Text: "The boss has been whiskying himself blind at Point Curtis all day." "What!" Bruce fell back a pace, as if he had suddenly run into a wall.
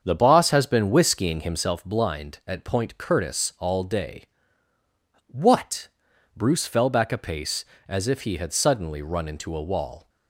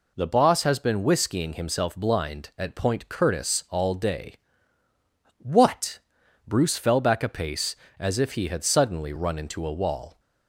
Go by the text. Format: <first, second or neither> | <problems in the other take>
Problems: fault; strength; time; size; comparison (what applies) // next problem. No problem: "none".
second | starts louder than the rest; until 1.8 s; 7 dB